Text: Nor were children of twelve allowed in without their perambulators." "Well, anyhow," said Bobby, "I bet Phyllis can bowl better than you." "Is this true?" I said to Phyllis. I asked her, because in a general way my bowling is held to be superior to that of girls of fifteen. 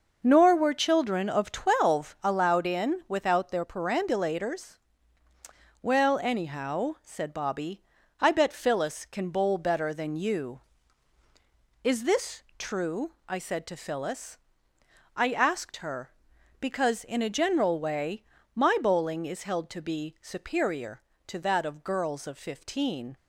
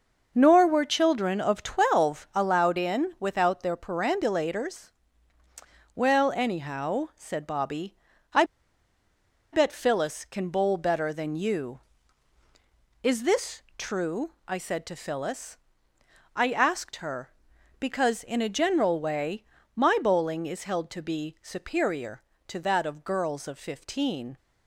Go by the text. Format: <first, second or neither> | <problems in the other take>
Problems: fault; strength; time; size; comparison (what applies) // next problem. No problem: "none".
first | pauses between "I" and "bet"; at 8.4 s; 1.0 s long // pauses between "this" and "true"; slight; at 13.6 s; 0.16 s long; slight in the first // pauses between "way" and "my"; slight; at 19.4 s; 0.32 s long; slight in the first